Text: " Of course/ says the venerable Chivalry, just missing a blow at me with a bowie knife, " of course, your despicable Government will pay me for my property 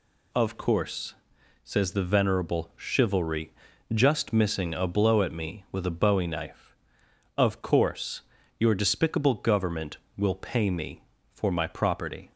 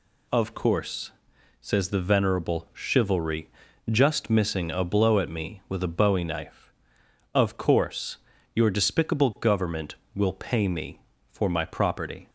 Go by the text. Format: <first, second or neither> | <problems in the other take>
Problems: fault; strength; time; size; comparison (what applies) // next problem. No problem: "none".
neither | none